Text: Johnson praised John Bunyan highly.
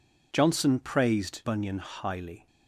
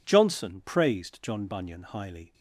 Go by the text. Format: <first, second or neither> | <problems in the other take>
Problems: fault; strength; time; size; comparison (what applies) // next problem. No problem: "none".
second | skips "John"; at 1.4 s